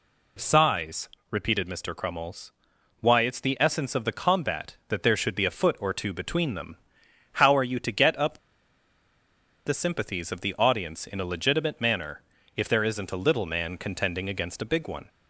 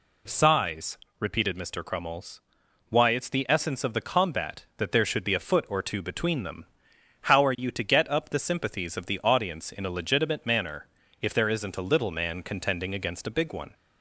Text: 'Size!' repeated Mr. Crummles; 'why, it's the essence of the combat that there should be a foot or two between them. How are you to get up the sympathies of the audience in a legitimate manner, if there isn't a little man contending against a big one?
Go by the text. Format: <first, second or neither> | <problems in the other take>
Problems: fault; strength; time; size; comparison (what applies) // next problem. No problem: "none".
second | pauses between "up" and "the"; strong; at 8.3 s; 1.2 s long